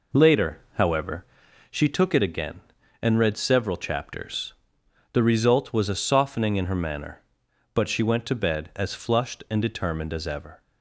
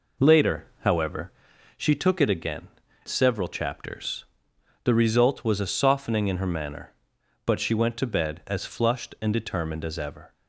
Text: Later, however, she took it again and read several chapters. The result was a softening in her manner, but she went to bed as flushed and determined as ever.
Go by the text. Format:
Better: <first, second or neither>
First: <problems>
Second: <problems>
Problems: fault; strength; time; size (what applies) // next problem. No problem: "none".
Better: first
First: none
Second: skips "and read"; at 2.8 s